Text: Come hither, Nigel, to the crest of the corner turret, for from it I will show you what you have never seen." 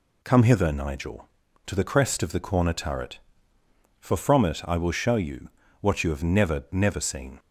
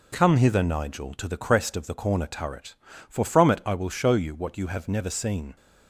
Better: second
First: pauses between "you" and "what"; slight; at 5.4 s; 0.32 s long // says "never" twice; at 6.7 s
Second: none

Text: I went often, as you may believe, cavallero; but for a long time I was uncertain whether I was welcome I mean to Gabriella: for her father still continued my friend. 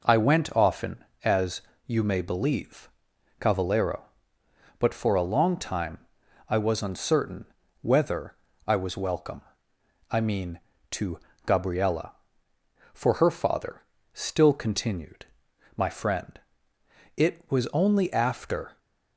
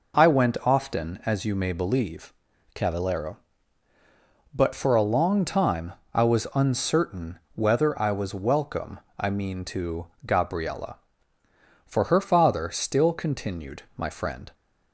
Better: second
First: pauses between "as" and "you"; slight; at 1.6 s; 0.24 s long // pauses between "time" and "I"; noticeable; at 5.9 s; 0.50 s long // pauses between "uncertain" and "whether"; slight; at 7.4 s; 0.36 s long // pauses between "whether" and "I"; slight; at 8.3 s; 0.30 s long // pauses between "welcome" and "I"; noticeable; at 9.4 s; 0.68 s long // pauses between "to" and "Gabriella"; slight; at 11.1 s; 0.26 s long // pauses between "father" and "still"; slight; at 13.8 s; 0.32 s long // pauses between "continued" and "my"; noticeable; at 15.2 s; 0.50 s long // goes on to say "It was only after"; from 17.1 s on; 1.6 s long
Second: pauses between "time" and "I"; slight; at 5.9 s; 0.22 s long // pauses between "uncertain" and "whether"; slight; at 7.3 s; 0.16 s long // pauses between "welcome" and "I"; slight; at 8.9 s; 0.20 s long // pauses between "to" and "Gabriella"; slight; at 10.0 s; 0.18 s long // pauses between "continued" and "my"; slight; at 13.8 s; 0.16 s long

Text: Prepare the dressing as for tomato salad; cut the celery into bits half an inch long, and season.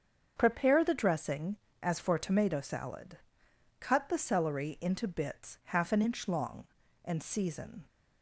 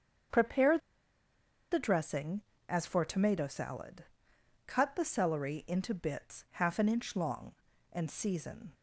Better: first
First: starts louder than the rest; until 1.3 s; 7 dB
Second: starts louder than the rest; until 2.2 s; 7 dB // pauses between "Prepare" and "the"; noticeable; at 0.7 s; 0.94 s long

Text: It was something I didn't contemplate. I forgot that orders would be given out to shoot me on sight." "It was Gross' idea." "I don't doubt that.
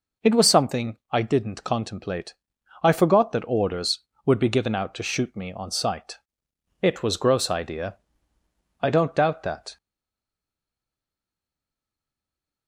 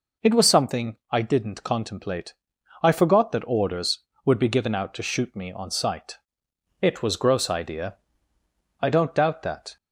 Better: second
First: pauses between "something" and "I"; slight; at 0.9 s; 0.16 s long // stays silent after the last word; strong; from 9.7 s on; 2.9 s long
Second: pauses between "something" and "I"; slight; at 0.9 s; 0.16 s long

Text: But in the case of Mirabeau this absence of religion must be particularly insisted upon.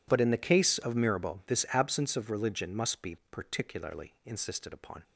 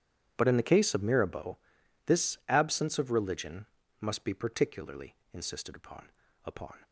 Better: first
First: none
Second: pauses between "Mirabeau" and "this"; noticeable; at 1.5 s; 0.48 s long // pauses between "religion" and "must"; slight; at 3.6 s; 0.34 s long // pauses between "particularly" and "insisted"; slight; at 5.1 s; 0.18 s long // says "upon" twice; at 6.4 s

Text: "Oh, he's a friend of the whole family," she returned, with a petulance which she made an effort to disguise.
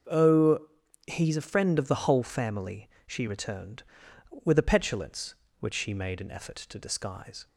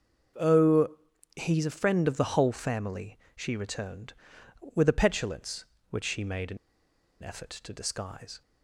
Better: first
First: starts louder than the rest; until 1.5 s; 6.5 dB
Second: starts louder than the rest; until 1.8 s; 6.5 dB // pauses between "an" and "effort"; noticeable; at 6.5 s; 0.65 s long

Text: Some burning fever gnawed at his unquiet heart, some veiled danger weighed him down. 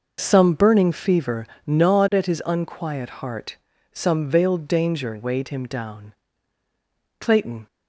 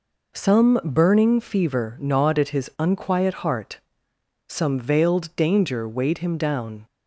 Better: second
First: pauses between "fever" and "gnawed"; slight; at 1.4 s; 0.18 s long // goes on to say "Clayton"; slight; from 7.1 s on; 0.48 s long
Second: none

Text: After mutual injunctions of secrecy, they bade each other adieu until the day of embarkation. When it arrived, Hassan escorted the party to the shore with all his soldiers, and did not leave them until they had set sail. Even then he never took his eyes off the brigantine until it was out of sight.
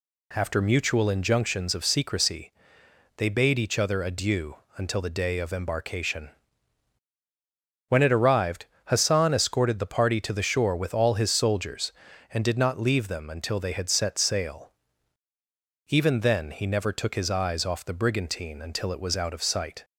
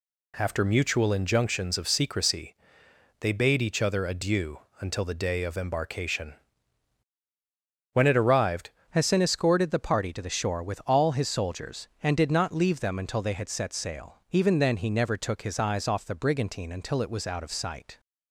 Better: first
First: pauses between "adieu" and "until"; slight; at 4.5 s; 0.22 s long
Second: pauses between "adieu" and "until"; slight; at 4.5 s; 0.22 s long // changes voice at "Hassan"; from 8.8 s on; 9.1 s long

